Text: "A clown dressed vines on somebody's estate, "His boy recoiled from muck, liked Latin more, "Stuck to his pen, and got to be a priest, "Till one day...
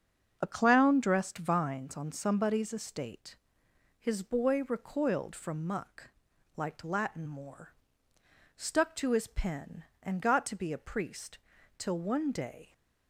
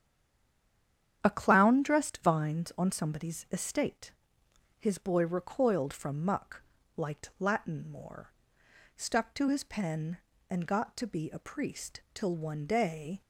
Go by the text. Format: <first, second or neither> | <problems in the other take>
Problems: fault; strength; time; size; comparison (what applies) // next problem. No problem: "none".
first | stays silent before the first word; noticeable; until 1.2 s; 1.2 s long // starts louder than the rest; strong; until 2.2 s; 9.5 dB; also in the first